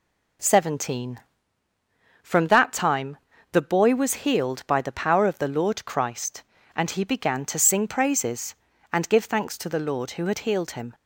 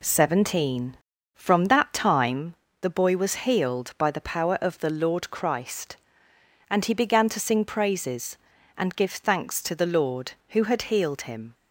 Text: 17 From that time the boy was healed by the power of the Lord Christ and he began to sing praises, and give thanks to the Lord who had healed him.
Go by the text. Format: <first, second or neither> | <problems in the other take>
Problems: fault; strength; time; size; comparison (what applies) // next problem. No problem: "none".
neither | pauses between "time" and "the"; slight; the same in both